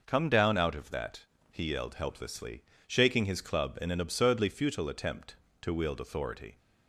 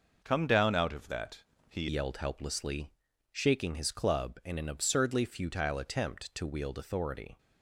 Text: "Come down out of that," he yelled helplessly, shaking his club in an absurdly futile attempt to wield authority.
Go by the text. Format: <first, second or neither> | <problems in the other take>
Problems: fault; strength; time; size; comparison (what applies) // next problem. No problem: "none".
first | changes voice at "yelled"; from 1.8 s on; 5.5 s long